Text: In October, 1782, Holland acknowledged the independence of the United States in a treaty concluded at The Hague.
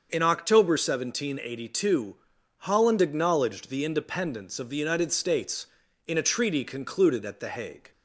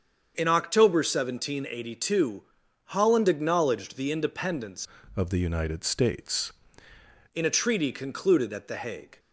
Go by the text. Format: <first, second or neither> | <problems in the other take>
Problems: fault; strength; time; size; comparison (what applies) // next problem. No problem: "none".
first | starts louder than the rest; strong; until 1.3 s; 7 dB; also in the first // changes voice from "of" to "States"; from 5.1 to 6.5 s; 1.4 s long